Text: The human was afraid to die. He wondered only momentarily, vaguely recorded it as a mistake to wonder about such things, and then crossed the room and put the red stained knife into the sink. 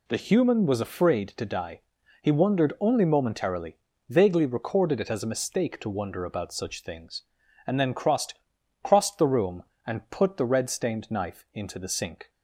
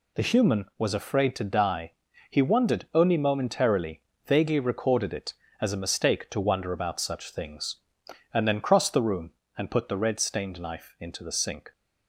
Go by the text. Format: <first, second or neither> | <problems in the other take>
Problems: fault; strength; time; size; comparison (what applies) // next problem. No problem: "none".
second | says "crossed" twice; at 8.8 s